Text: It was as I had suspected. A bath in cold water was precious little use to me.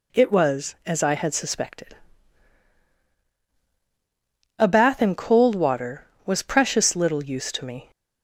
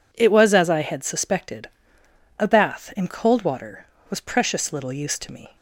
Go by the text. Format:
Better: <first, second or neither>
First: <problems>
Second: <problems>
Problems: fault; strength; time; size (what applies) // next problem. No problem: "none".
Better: neither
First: none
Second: none